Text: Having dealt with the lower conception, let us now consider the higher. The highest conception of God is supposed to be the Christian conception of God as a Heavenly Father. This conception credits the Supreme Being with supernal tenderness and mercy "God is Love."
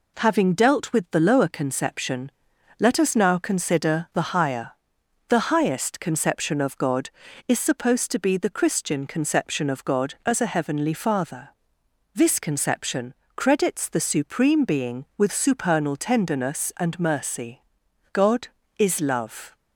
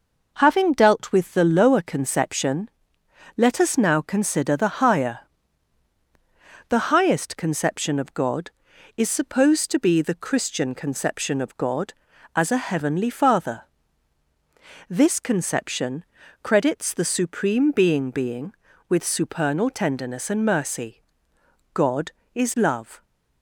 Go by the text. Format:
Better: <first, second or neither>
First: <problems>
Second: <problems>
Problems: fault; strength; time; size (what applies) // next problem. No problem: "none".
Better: first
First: pauses between "conception" and "credits"; slight; at 13.1 s; 0.22 s long // pauses between "mercy" and "God"; noticeable; at 17.6 s; 0.50 s long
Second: pauses between "conception" and "credits"; at 16.0 s; 0.40 s long // says "Being" twice; at 18.1 s // pauses between "mercy" and "God"; noticeable; at 21.0 s; 0.72 s long